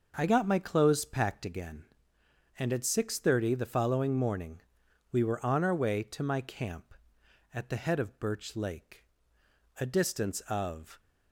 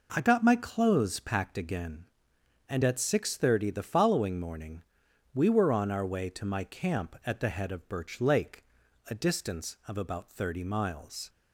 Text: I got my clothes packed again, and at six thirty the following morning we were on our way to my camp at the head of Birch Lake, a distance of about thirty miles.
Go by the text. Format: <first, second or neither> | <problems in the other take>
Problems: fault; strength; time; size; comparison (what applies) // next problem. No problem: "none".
second | pauses between "morning" and "we"; noticeable; at 4.6 s; 0.50 s long; noticeable in the second // stops before "about thirty miles"; at 10.9 s